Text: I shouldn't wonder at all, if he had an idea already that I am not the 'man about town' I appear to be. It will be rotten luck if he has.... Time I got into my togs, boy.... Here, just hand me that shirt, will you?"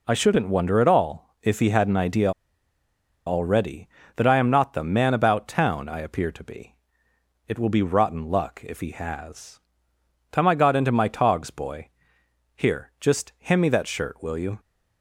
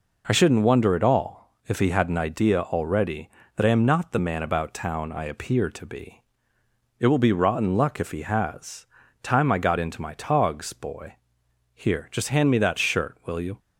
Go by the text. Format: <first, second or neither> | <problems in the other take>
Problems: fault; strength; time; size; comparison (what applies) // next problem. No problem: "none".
second | pauses between "idea" and "already"; noticeable; at 2.3 s; 0.96 s long